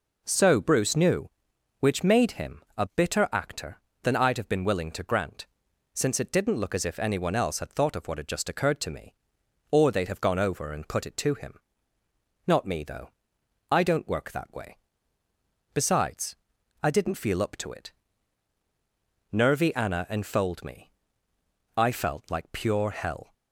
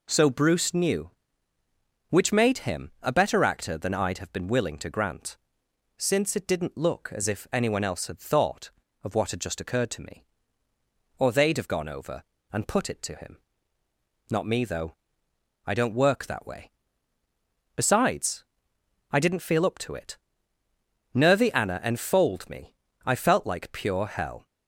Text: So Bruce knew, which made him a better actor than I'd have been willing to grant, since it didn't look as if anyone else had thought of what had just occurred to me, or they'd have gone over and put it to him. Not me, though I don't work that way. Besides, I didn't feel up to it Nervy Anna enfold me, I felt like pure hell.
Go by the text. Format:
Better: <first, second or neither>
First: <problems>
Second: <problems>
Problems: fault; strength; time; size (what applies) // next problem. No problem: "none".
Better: second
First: pauses between "him" and "a"; slight; at 2.6 s; 0.16 s long // says "bitter" for "better"; at 2.8 s // pauses between "though" and "I"; noticeable; at 13.0 s; 0.62 s long // pauses between "it" and "Nervy"; strong; at 17.9 s; 1.4 s long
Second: pauses between "though" and "I"; noticeable; at 14.9 s; 0.70 s long // pauses between "it" and "Nervy"; noticeable; at 20.1 s; 0.96 s long